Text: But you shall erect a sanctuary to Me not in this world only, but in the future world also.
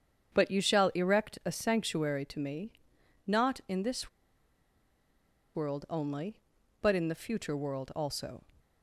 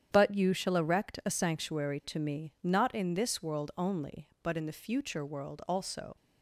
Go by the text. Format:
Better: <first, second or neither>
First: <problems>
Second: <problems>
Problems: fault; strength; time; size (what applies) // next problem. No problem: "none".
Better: second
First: starts louder than the rest; strong; until 1.3 s; 8 dB // pauses between "Me" and "not"; noticeable; at 2.7 s; 0.54 s long // pauses between "this" and "world"; strong; at 4.0 s; 1.4 s long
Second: starts louder than the rest; strong; until 1.1 s; 9 dB